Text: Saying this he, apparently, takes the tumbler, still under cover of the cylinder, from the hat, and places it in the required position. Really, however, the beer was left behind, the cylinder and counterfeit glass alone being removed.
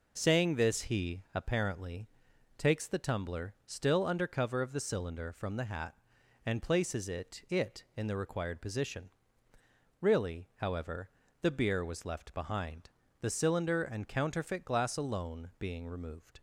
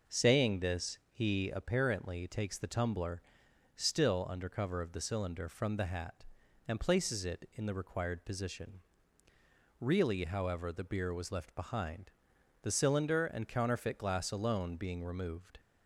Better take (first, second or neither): second